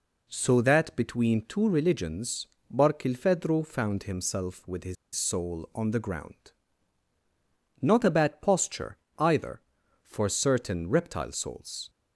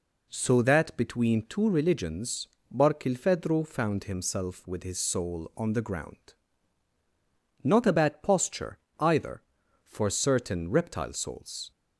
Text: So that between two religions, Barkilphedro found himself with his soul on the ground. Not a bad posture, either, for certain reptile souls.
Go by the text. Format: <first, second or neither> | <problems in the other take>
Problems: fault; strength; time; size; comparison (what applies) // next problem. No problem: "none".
second | pauses between "his" and "soul"; slight; at 4.9 s; 0.20 s long